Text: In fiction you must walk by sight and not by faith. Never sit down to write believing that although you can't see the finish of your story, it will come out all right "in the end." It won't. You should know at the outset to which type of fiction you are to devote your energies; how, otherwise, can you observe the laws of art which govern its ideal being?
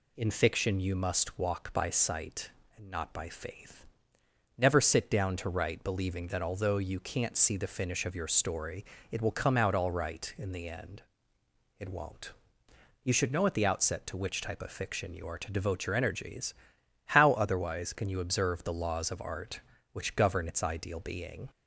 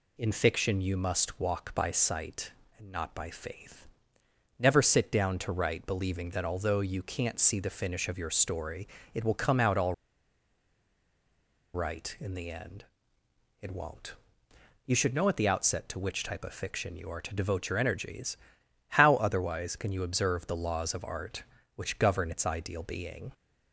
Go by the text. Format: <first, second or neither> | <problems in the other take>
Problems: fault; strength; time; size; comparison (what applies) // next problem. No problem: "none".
first | pauses between "all" and "right"; strong; at 9.9 s; 1.8 s long